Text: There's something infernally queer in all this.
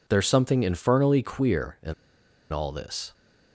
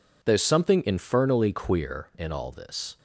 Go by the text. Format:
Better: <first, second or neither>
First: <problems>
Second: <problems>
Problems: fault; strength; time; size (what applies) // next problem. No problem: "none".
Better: second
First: pauses between "in" and "all"; noticeable; at 1.9 s; 0.59 s long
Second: none